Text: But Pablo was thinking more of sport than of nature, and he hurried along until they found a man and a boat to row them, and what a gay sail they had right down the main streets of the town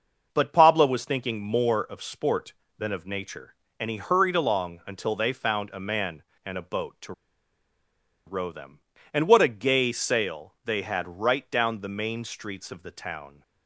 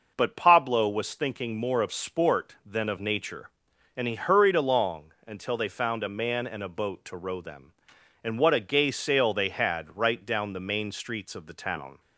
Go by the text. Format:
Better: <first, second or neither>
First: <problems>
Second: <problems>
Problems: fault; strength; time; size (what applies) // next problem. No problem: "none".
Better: second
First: pauses between "to" and "row"; at 7.1 s; 1.1 s long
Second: none